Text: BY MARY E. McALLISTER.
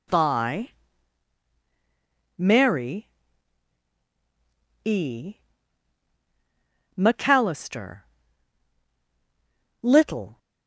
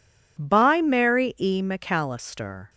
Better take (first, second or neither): second